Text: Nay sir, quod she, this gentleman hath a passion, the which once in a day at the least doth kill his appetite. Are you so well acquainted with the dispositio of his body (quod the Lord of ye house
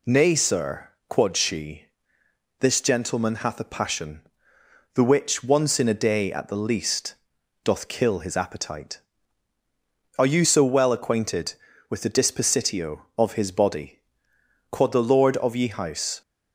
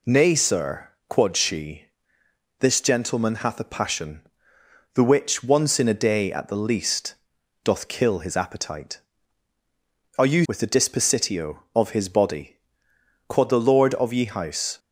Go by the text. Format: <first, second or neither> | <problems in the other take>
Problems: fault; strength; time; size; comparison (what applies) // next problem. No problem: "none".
first | pauses between "least" and "doth"; noticeable; at 7.1 s; 0.50 s long; noticeable in the first // skips "so well acquainted"; at 10.4 s